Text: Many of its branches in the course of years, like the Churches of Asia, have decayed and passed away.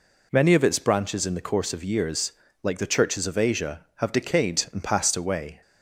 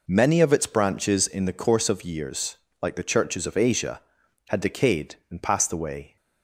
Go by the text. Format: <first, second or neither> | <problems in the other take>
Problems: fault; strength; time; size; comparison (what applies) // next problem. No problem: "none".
first | says "had" for "have"; at 4.4 s